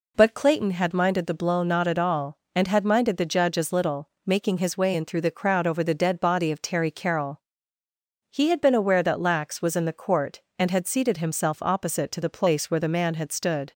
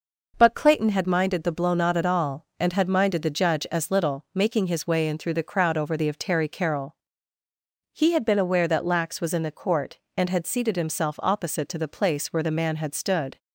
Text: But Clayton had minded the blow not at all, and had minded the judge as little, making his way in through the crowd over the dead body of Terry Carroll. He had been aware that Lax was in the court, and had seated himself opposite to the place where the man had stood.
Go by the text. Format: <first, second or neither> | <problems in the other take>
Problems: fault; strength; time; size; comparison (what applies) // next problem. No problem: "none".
first | skips "dead body"; at 6.0 s